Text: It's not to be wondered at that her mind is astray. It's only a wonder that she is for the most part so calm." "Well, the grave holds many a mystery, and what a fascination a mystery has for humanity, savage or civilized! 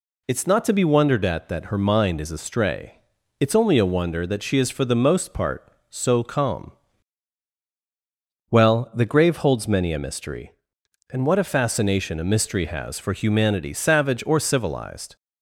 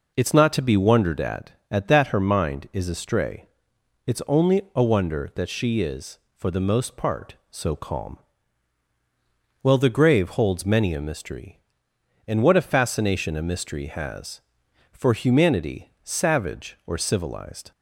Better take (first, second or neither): first